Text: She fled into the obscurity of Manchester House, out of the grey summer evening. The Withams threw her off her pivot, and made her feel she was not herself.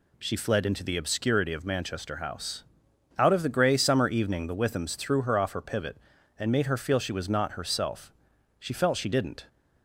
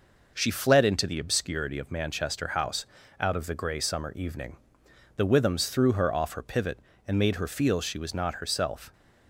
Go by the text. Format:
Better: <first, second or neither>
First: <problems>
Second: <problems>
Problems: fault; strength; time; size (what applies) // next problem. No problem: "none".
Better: second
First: goes on to say "She felt she didn't"; noticeable; from 8.5 s on; 0.86 s long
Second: none